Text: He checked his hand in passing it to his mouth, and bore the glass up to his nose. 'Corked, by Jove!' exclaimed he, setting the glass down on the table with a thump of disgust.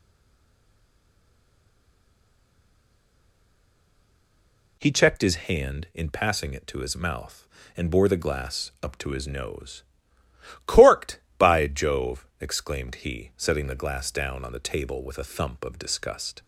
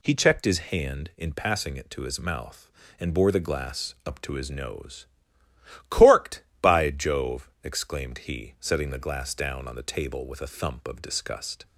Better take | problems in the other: second | stays silent before the first word; strong; until 4.7 s; 4.7 s long

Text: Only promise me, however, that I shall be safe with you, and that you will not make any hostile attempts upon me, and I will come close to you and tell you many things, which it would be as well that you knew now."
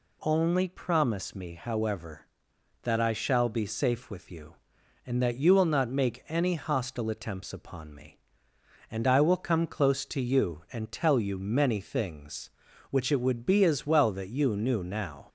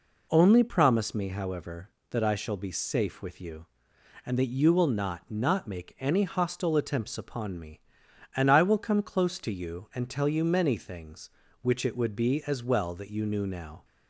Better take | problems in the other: first | says "not" twice; at 5.2 s

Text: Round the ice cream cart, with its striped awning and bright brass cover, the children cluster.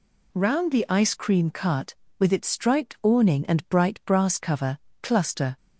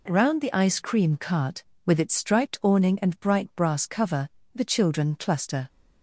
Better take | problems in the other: second | skips "the children"; at 4.9 s

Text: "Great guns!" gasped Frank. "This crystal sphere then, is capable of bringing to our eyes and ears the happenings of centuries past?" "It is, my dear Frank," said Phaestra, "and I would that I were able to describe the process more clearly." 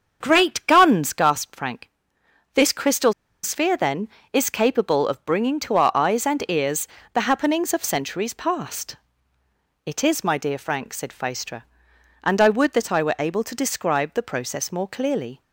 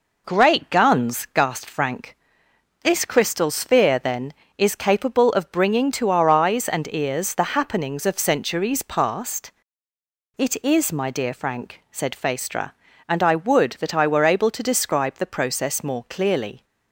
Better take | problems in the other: second | starts louder than the rest; until 1.2 s; 7 dB // pauses between "crystal" and "sphere"; slight; at 3.1 s; 0.31 s long // pauses between "ears" and "the"; slight; at 6.8 s; 0.26 s long

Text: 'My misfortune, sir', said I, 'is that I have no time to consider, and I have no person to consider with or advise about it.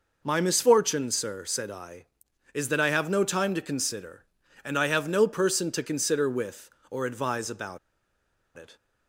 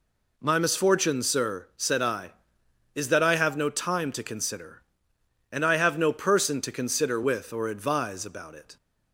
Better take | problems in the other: second | pauses between "about" and "it"; noticeable; at 7.7 s; 0.78 s long

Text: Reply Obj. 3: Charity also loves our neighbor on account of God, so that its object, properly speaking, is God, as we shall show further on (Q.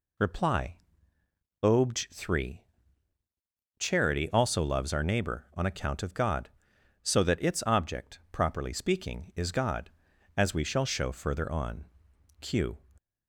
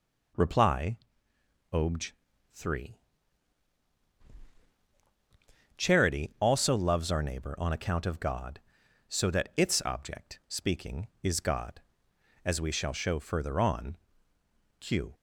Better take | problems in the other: first | pauses between "Reply" and "Obj"; noticeable; at 0.9 s; 0.74 s long; noticeable in the first // skips "properly"; at 10.4 s

